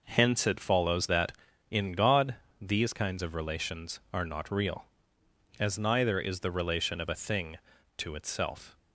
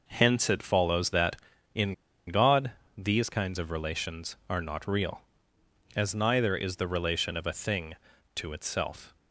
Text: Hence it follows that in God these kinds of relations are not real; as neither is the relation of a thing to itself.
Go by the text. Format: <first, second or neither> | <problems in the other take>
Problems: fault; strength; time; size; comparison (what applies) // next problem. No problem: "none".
first | pauses between "in" and "God"; slight; at 1.9 s; 0.33 s long // pauses between "God" and "these"; slight; at 2.7 s; 0.26 s long; slight in the first